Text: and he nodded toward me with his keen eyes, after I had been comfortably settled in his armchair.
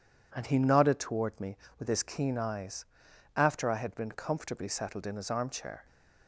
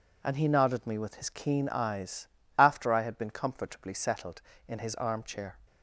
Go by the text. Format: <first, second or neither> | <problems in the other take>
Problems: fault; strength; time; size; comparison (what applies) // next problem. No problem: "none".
first | skips "toward"; at 0.8 s